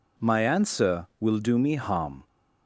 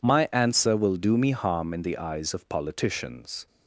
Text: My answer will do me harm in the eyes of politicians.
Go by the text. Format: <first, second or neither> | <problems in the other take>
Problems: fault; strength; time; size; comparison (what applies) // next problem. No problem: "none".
second | stops before "in the eyes of politicians"; at 2.2 s